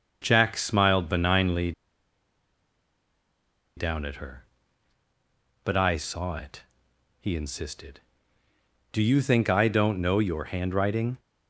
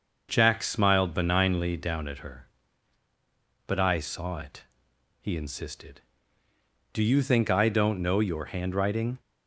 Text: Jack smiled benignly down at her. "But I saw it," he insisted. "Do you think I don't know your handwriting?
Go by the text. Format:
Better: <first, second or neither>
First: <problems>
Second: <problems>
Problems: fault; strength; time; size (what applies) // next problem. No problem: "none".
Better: second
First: starts louder than the rest; noticeable; until 1.2 s; 6 dB // pauses between "benignly" and "down"; strong; at 1.7 s; 2.0 s long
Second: starts louder than the rest; noticeable; until 1.3 s; 6 dB